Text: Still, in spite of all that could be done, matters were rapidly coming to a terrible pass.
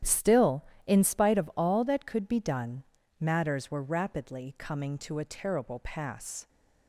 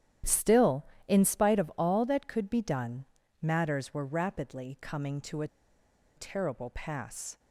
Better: first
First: starts louder than the rest; strong; until 1.2 s; 10.5 dB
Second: starts louder than the rest; strong; until 1.4 s; 10.5 dB // pauses between "a" and "terrible"; noticeable; at 5.4 s; 0.69 s long

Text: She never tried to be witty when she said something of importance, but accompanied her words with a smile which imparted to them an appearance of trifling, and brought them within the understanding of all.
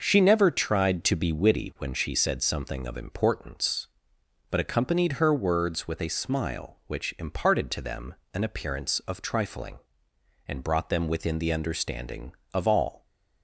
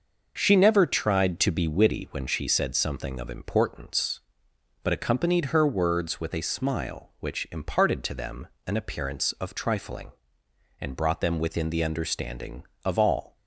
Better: neither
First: pauses between "them" and "an"; slight; at 8.1 s; 0.20 s long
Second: pauses between "them" and "an"; slight; at 8.4 s; 0.20 s long

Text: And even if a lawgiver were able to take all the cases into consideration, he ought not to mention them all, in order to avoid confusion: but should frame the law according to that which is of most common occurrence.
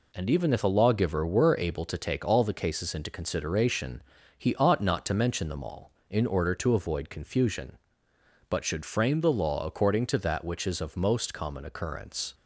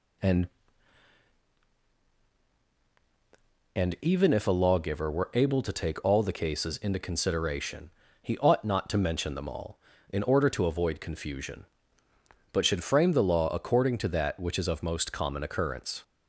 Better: first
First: none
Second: says "And" twice; at 3.7 s

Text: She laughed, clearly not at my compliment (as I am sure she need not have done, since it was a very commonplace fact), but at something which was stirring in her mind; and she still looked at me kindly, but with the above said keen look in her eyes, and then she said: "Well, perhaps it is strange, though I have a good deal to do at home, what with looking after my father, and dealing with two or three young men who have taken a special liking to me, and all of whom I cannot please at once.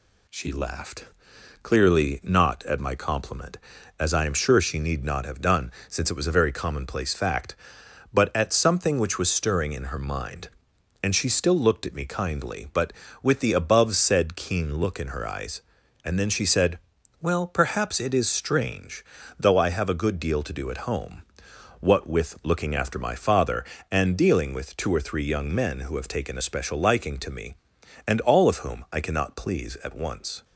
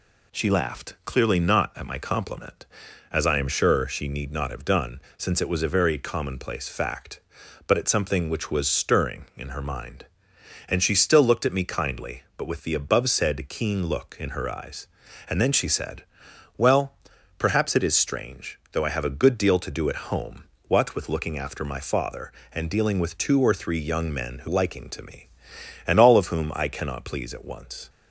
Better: first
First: none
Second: skips "have taken a special"; at 24.4 s

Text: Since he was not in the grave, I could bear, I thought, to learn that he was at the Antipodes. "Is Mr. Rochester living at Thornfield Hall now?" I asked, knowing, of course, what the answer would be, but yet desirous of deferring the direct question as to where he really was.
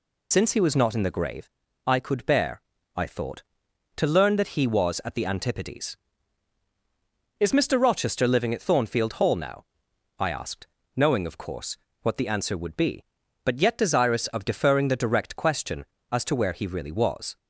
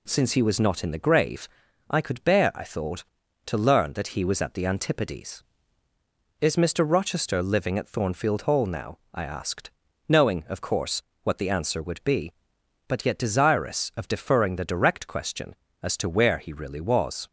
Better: second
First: loses the start of "Since"; at 0.3 s; 70 ms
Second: none

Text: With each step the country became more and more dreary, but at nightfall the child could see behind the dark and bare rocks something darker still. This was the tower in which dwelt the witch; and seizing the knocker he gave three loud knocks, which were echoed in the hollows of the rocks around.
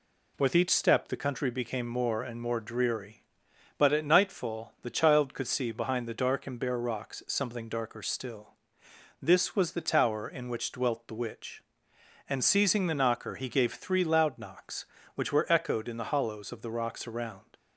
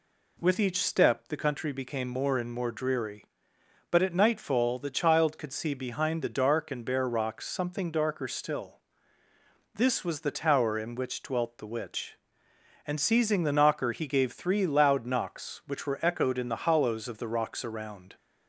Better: neither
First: none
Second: none

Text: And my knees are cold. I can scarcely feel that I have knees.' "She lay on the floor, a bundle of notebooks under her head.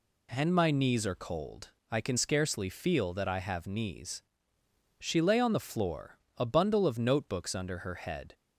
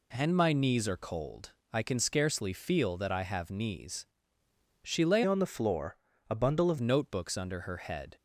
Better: first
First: none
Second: changes voice from "on" to "of"; from 5.2 to 6.7 s; 1.5 s long

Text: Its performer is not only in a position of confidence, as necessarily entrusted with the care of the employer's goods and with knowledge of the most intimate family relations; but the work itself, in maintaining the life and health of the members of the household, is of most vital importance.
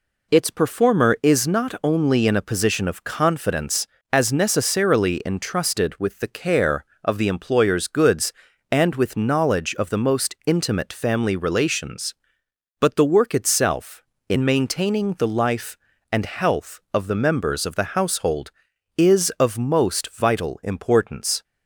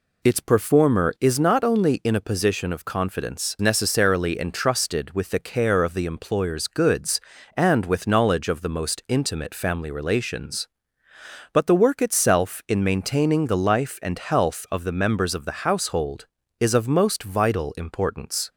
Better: first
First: none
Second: skips "as"; at 3.5 s

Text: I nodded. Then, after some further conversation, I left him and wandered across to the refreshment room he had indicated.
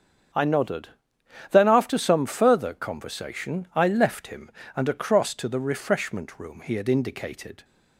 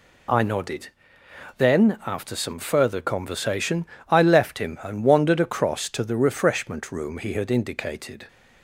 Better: second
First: starts louder than the rest; strong; until 1.9 s; 7.5 dB // skips "wandered"; at 4.8 s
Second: none

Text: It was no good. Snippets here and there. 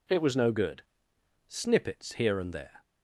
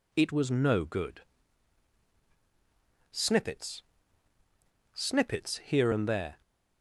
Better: first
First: none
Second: says "Snippets" twice; at 4.9 s

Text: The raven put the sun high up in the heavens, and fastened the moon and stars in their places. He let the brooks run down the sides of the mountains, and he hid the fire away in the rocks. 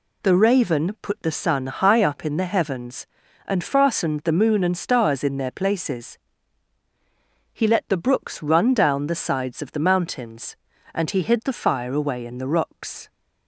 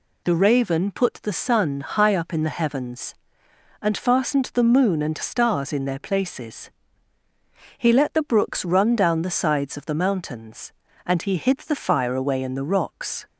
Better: neither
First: none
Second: none

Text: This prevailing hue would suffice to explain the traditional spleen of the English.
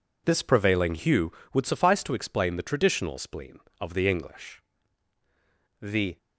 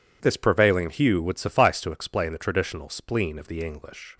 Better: second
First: goes on to say "The"; slight; from 5.8 s on; 0.36 s long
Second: none

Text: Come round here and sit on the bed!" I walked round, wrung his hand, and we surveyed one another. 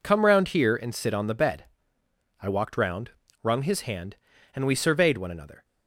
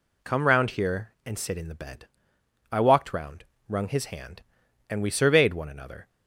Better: first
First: none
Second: says "in" for "on"; at 1.5 s

